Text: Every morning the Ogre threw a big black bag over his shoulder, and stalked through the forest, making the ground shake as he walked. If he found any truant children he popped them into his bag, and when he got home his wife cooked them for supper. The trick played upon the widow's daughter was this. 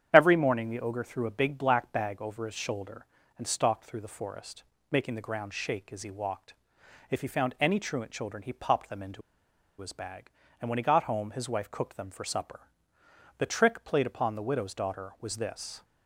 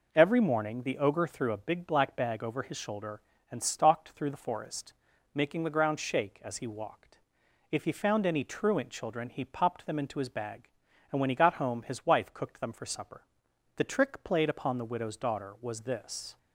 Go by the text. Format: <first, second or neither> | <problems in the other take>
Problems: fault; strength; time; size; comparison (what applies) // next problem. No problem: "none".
second | starts louder than the rest; strong; until 1.1 s; 9 dB // pauses between "into" and "his"; noticeable; at 9.2 s; 0.58 s long